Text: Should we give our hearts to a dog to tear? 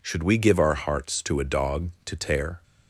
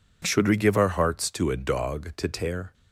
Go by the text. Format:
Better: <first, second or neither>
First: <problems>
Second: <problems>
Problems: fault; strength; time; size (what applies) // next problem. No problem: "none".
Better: neither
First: none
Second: none